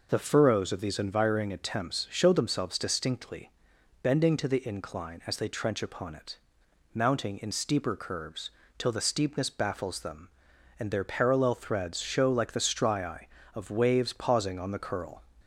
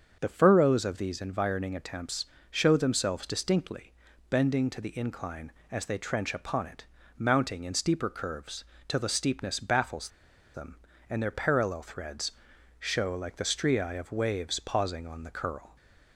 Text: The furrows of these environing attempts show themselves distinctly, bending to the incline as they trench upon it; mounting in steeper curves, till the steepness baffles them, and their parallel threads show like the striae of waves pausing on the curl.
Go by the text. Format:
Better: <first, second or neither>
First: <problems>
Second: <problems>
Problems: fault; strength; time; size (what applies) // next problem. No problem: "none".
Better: first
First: none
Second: starts louder than the rest; until 1.2 s; 7 dB // pauses between "attempts" and "show"; slight; at 2.2 s; 0.24 s long // pauses between "baffles" and "them"; at 10.0 s; 0.45 s long // pauses between "threads" and "show"; noticeable; at 12.3 s; 0.46 s long